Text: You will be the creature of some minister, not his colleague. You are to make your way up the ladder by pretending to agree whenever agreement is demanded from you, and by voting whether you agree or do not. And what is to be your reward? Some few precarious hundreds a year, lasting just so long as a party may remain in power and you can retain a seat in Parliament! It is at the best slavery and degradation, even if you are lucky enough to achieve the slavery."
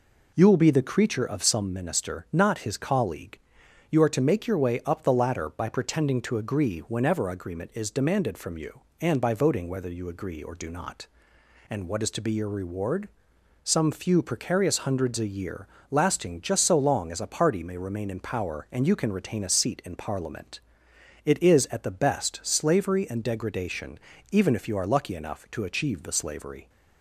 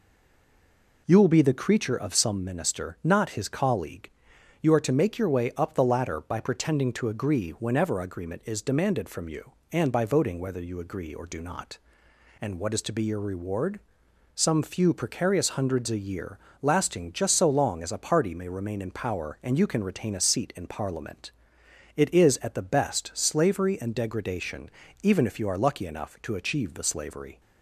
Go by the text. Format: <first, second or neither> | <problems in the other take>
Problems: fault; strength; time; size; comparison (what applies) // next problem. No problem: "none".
first | stays silent before the first word; until 1.0 s; 1.0 s long